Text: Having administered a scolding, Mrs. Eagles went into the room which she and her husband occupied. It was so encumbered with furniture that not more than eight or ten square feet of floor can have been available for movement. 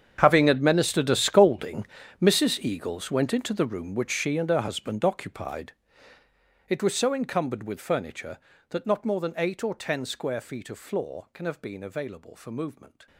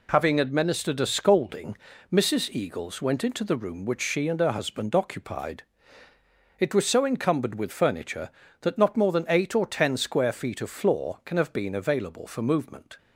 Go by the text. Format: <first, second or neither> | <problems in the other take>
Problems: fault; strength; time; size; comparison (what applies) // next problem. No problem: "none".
second | gets quieter; strong; throughout; 18 dB